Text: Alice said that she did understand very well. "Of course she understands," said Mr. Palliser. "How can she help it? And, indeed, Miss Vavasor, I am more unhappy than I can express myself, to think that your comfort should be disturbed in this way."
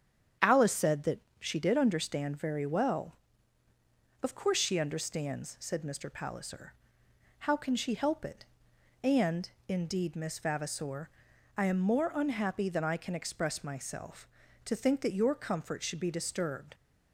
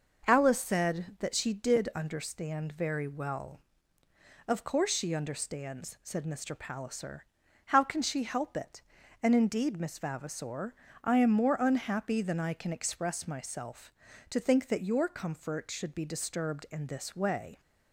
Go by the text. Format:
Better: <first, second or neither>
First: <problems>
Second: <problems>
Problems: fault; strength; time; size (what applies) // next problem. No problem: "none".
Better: second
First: starts louder than the rest; strong; until 1.6 s; 8.5 dB // pauses between "that" and "she"; slight; at 1.1 s; 0.20 s long // stops before "in this way"; at 16.7 s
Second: none